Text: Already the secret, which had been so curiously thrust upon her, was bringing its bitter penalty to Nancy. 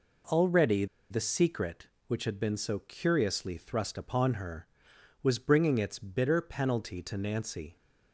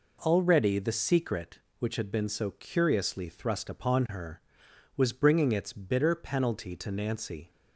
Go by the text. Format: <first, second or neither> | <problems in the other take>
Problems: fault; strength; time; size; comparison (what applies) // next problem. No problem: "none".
second | pauses between "Already" and "the"; slight; at 0.8 s; 0.24 s long